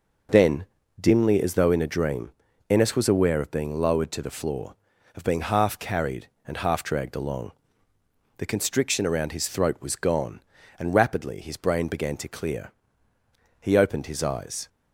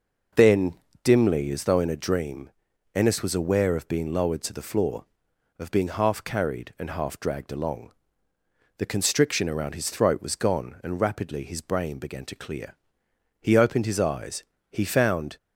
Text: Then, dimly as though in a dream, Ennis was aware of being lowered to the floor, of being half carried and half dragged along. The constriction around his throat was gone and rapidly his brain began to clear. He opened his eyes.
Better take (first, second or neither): first